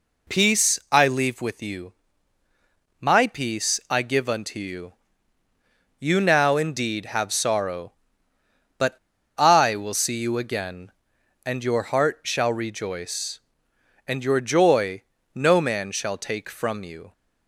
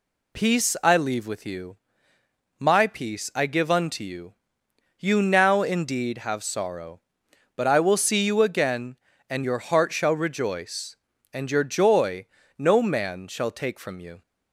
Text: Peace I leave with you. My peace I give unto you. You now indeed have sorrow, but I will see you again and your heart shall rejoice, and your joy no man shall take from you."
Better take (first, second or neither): second